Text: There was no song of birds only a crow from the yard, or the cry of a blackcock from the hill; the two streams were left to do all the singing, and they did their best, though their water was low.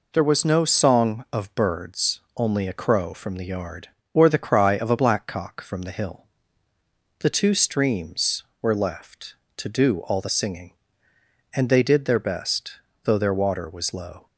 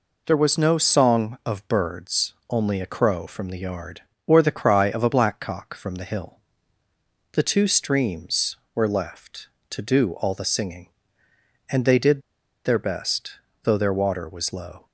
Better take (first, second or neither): first